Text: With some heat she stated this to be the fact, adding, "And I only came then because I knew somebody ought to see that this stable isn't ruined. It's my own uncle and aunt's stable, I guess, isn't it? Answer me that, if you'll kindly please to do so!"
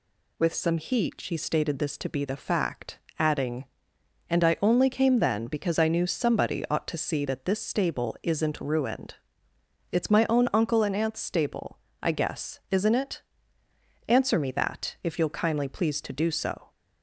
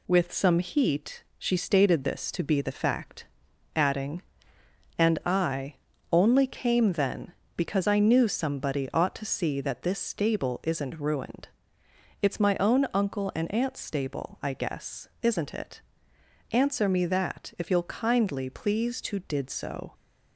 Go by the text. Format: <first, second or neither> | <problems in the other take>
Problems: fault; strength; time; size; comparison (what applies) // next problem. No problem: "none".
first | pauses between "I" and "only"; slight; at 5.7 s; 0.36 s long // says "did" for "do"; at 19.1 s